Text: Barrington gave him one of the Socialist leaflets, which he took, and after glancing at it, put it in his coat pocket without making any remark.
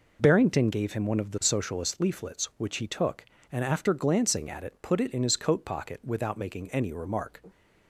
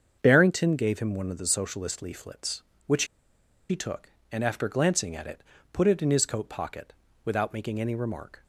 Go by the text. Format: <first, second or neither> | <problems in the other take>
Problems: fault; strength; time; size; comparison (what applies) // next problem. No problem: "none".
first | starts louder than the rest; until 1.2 s; 7 dB // pauses between "which" and "he"; noticeable; at 3.0 s; 0.65 s long // pauses between "pocket" and "without"; slight; at 6.9 s; 0.30 s long